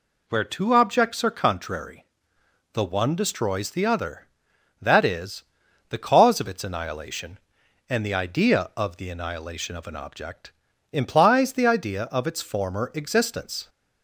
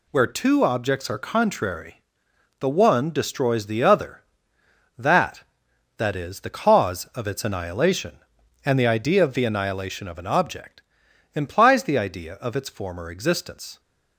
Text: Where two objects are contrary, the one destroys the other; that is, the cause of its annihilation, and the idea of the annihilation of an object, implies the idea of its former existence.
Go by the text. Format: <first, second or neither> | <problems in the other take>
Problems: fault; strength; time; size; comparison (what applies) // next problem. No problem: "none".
first | says "that" twice; at 5.9 s